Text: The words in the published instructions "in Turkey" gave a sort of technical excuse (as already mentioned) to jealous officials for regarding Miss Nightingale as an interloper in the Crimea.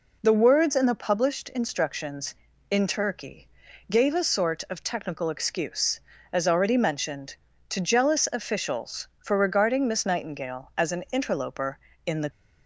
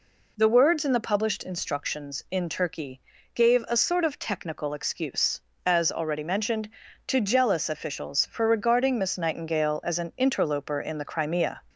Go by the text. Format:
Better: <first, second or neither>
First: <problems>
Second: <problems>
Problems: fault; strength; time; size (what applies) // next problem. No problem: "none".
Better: second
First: pauses between "Turkey" and "gave"; at 3.4 s; 0.42 s long // stops before "Crimea"; at 12.2 s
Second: pauses between "Turkey" and "gave"; slight; at 3.0 s; 0.34 s long